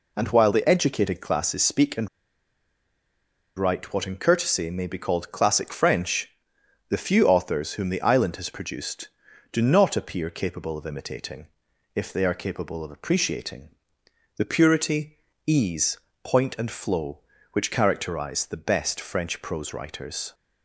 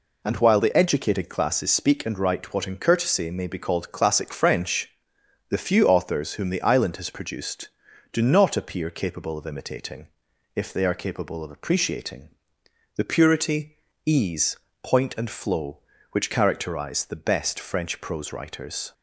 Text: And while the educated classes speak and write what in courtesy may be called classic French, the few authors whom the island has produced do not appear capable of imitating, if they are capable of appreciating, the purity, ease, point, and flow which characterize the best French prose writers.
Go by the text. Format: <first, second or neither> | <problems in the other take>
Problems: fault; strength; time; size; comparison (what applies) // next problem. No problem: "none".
second | pauses between "and" and "write"; strong; at 2.0 s; 1.4 s long